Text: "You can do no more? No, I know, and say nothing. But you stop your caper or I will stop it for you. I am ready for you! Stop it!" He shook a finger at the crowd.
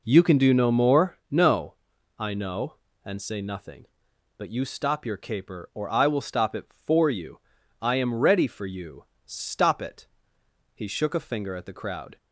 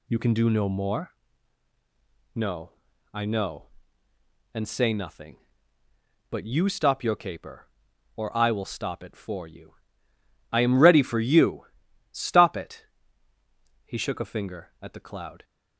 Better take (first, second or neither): first